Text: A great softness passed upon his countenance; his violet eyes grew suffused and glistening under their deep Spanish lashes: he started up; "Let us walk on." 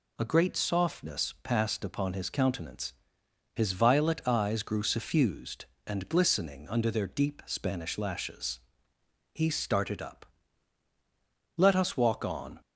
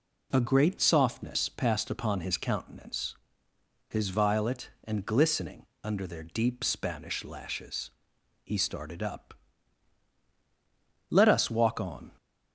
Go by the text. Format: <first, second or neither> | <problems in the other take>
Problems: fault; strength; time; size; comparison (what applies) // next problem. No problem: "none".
first | skips "eyes grew suffused"; at 4.7 s // pauses between "glistening" and "under"; slight; at 5.6 s; 0.18 s long